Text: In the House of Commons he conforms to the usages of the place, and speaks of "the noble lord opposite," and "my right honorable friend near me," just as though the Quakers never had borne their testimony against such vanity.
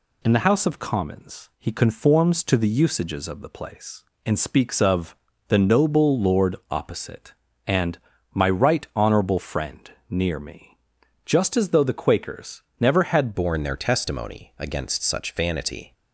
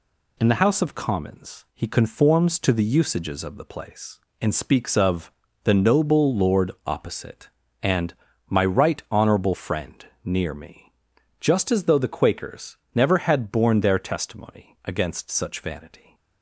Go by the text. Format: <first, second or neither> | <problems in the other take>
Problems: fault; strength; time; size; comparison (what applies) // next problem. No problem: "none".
second | pauses between "of" and "the"; slight; at 5.1 s; 0.32 s long; slight in the second // pauses between "lord" and "opposite"; slight; at 6.5 s; 0.16 s long; slight in the second // pauses between "and" and "my"; slight; at 7.9 s; 0.34 s long; slight in the second // pauses between "friend" and "near"; slight; at 9.8 s; 0.20 s long; slight in the second // pauses between "Quakers" and "never"; slight; at 12.6 s; 0.18 s long; slight in the second // changes voice at "borne"; from 13.3 s on; 2.6 s long